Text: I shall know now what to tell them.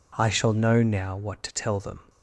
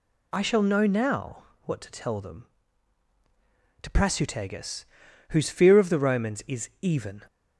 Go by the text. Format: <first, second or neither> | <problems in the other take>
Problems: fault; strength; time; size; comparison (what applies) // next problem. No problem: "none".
first | pauses between "now" and "what"; slight; at 1.4 s; 0.22 s long // goes on to say "To Prasutagus whose fear of the Romans is even"; strong; from 3.8 s on; 3.4 s long